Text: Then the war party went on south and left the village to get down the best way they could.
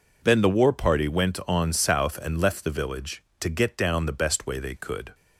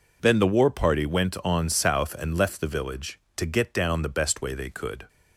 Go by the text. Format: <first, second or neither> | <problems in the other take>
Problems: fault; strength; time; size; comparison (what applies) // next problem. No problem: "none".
neither | none